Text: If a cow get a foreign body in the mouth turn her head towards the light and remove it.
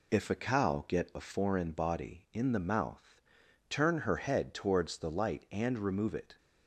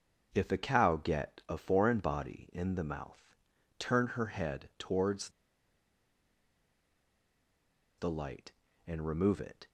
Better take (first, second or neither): first